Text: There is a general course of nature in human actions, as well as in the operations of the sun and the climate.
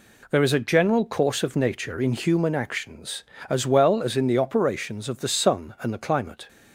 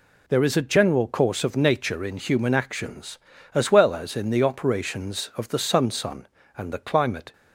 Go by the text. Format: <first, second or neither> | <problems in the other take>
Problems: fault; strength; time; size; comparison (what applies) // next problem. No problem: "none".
first | says "sun" twice; at 5.8 s